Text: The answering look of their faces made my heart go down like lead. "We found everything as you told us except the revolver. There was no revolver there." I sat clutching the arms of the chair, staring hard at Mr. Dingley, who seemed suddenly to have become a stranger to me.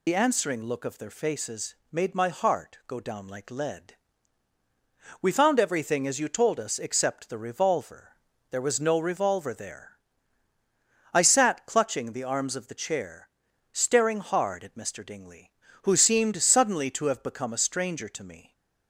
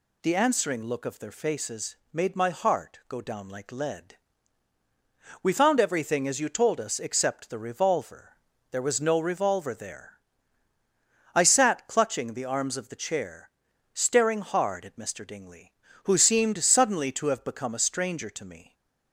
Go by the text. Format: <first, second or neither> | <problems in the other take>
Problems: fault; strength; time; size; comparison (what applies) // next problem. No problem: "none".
second | loses the start of "The"; at 0.0 s; 55 ms // pauses between "faces" and "made"; slight; at 1.7 s; 0.16 s long; slight in the second